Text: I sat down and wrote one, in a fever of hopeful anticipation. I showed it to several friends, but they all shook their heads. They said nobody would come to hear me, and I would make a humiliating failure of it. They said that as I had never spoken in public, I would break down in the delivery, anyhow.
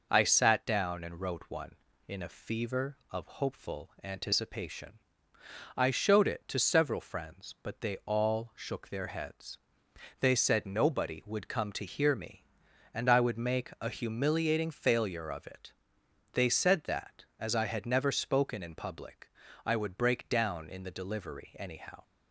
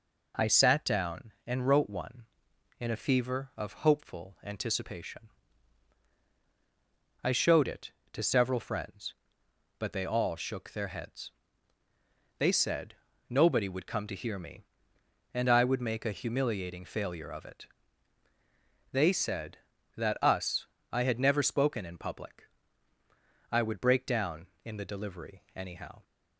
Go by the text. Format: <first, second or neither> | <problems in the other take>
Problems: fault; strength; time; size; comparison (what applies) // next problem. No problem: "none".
first | pauses between "said" and "nobody"; slight; at 12.9 s; 0.33 s long // says "us" for "as"; at 20.2 s